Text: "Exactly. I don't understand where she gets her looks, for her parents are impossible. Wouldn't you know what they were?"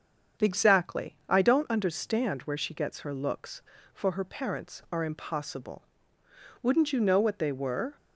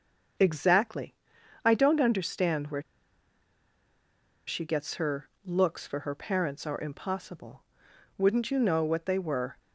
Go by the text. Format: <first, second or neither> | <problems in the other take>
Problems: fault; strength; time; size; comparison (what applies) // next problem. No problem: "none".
first | starts louder than the rest; strong; until 1.8 s; 7 dB; strong in the first // pauses between "where" and "she"; strong; at 2.8 s; 1.6 s long // pauses between "her" and "looks"; slight; at 5.2 s; 0.16 s long